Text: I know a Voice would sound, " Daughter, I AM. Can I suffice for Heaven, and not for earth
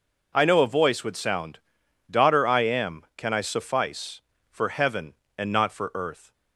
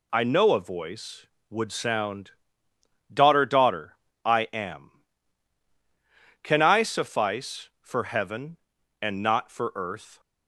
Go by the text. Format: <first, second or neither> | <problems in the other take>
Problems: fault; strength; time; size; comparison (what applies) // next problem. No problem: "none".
first | says "Daughter" twice; at 3.4 s